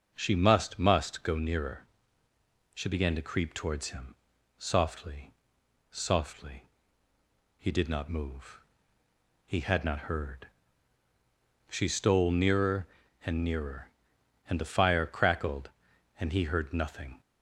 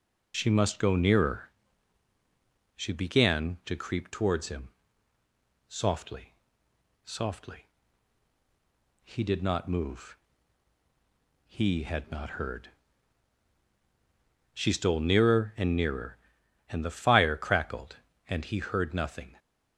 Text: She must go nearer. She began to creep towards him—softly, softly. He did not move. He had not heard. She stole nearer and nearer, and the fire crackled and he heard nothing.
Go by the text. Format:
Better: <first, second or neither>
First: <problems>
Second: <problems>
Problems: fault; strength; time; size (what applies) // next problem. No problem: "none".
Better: second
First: starts louder than the rest; until 1.1 s; 6.5 dB // says "must" twice; at 0.7 s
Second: none